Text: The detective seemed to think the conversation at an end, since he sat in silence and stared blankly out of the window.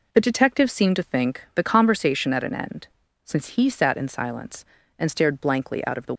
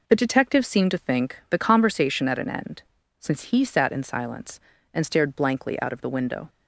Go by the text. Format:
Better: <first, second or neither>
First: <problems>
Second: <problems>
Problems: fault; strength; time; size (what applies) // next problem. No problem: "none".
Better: second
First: stops before "window"; at 6.1 s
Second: none